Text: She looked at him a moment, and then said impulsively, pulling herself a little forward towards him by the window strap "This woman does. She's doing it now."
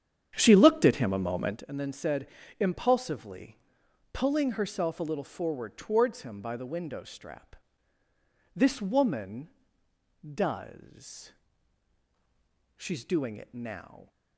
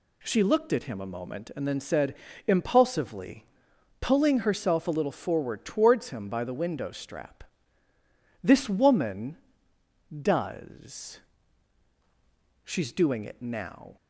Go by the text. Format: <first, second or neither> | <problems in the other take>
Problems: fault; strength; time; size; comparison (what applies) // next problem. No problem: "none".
second | starts louder than the rest; strong; until 1.7 s; 9 dB // pauses between "said" and "impulsively"; slight; at 2.2 s; 0.32 s long; slight in the second // pauses between "strap" and "This"; at 7.5 s; 1.0 s long; also in the second